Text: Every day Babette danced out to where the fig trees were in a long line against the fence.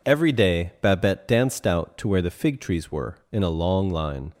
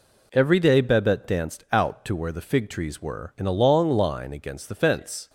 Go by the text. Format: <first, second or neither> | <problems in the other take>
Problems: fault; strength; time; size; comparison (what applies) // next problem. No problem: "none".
second | stops before "against the fence"; at 4.3 s